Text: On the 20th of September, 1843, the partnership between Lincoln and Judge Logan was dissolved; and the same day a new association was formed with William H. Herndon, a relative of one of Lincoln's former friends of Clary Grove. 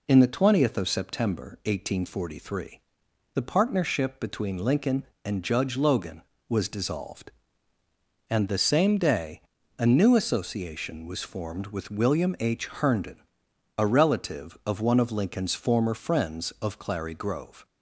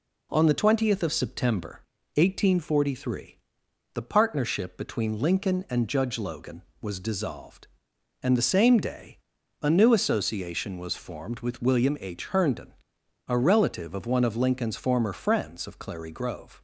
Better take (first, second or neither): second